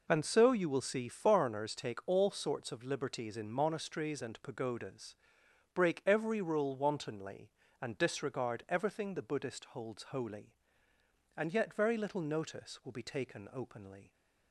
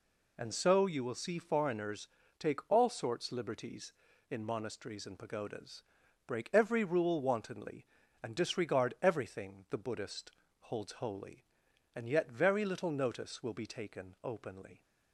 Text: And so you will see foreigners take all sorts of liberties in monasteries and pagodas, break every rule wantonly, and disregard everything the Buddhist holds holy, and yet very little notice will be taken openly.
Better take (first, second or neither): first